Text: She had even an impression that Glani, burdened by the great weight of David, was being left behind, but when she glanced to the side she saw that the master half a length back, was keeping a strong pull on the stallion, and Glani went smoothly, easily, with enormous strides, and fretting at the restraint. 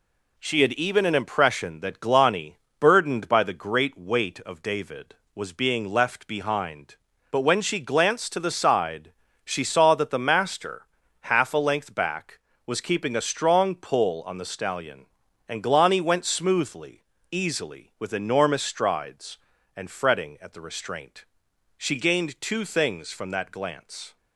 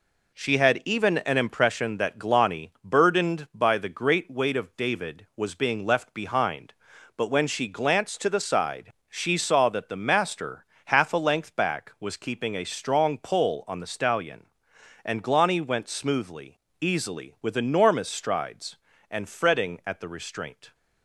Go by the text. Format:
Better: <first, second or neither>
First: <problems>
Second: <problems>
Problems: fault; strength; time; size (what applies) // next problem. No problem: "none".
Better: second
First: pauses between "side" and "she"; slight; at 9.1 s; 0.32 s long // pauses between "master" and "half"; slight; at 10.8 s; 0.36 s long // goes on to say "She gained two things from that glance"; strong; from 21.7 s on; 2.4 s long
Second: pauses between "side" and "she"; slight; at 8.9 s; 0.16 s long // pauses between "master" and "half"; slight; at 10.6 s; 0.20 s long